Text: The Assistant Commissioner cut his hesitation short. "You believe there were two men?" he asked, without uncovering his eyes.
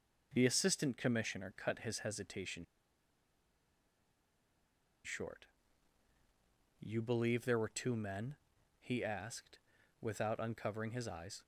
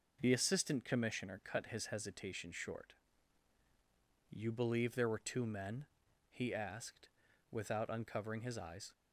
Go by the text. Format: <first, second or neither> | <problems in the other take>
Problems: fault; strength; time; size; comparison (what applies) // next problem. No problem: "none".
second | pauses between "hesitation" and "short"; strong; at 2.6 s; 2.4 s long